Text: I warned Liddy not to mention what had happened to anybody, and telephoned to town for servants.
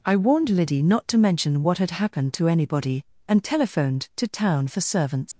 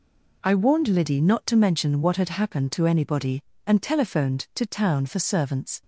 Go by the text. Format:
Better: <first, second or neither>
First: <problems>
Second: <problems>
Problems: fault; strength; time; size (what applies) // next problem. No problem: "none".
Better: second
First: leaves "servants" unfinished; at 5.3 s; 115 ms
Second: none